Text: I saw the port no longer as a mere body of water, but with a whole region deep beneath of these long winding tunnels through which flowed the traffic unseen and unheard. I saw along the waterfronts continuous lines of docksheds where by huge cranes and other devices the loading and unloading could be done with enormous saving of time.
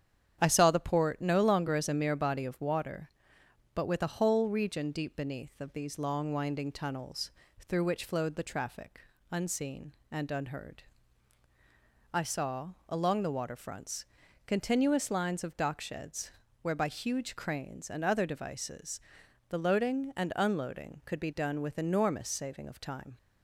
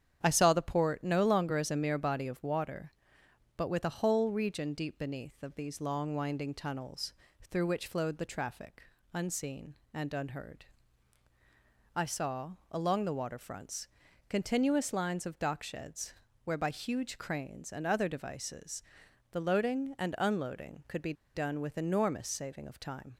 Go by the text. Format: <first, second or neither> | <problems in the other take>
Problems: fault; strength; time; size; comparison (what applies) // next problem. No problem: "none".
first | starts louder than the rest; strong; until 1.2 s; 9 dB; strong in the first // pauses between "tunnels" and "through"; at 7.1 s; 0.38 s long; also in the first // pauses between "traffic" and "unseen"; slight; at 8.8 s; 0.28 s long; slight in the first // pauses between "saw" and "along"; slight; at 12.5 s; 0.18 s long; slight in the first // pauses between "waterfronts" and "continuous"; at 13.8 s; 0.40 s long; also in the first // pauses between "docksheds" and "where"; slight; at 16.1 s; 0.32 s long; slight in the first // pauses between "devices" and "the"; noticeable; at 18.8 s; 0.48 s long; noticeable in the first // pauses between "be" and "done"; slight; at 21.1 s; 0.21 s long